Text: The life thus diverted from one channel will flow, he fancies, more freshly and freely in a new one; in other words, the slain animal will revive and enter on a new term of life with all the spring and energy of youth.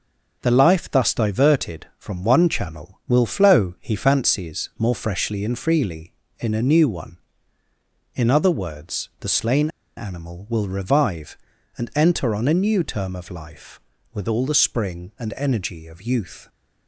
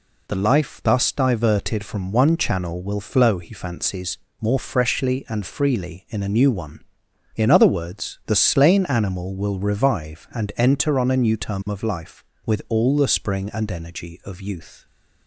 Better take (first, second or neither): second